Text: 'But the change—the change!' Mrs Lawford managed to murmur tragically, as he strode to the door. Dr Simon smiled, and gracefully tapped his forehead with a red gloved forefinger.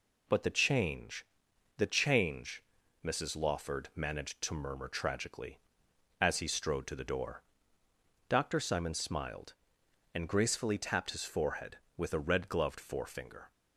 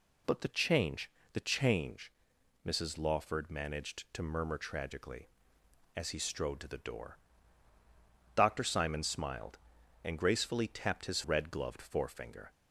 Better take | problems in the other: first | skips "forehead with a"; at 11.2 s

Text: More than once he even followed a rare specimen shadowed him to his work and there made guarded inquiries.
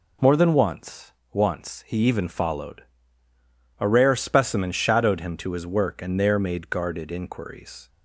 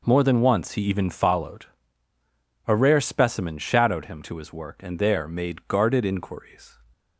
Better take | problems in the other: second | says "once" twice; at 1.3 s // pauses between "followed" and "a"; noticeable; at 2.8 s; 0.97 s long; also in the second

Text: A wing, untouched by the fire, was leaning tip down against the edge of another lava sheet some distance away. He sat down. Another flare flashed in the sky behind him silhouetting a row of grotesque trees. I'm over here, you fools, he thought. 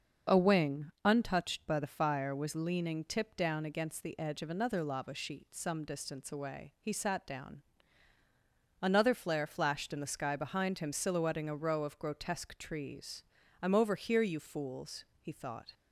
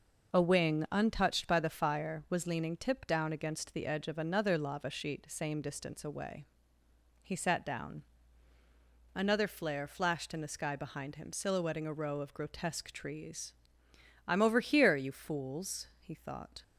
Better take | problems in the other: first | says "same" for "some"; at 5.2 s

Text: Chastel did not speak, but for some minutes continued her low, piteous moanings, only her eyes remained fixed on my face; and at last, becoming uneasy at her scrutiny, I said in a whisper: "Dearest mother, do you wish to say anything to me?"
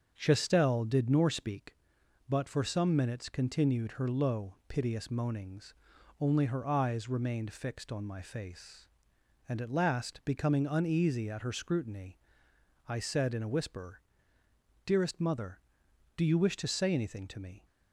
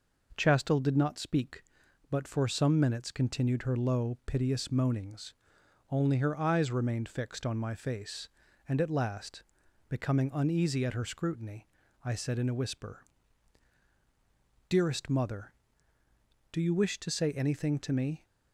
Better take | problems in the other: second | starts louder than the rest; until 1.1 s; 6.5 dB // says "nor" for "not"; at 1.0 s

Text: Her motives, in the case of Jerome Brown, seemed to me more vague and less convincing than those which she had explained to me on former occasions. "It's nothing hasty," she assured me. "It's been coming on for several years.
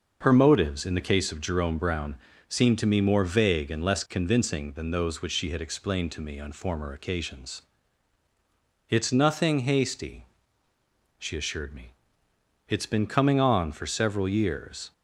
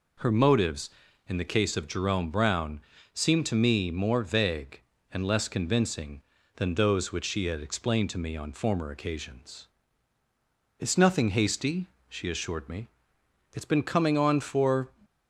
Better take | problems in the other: first | stops before "several years"; at 15.0 s

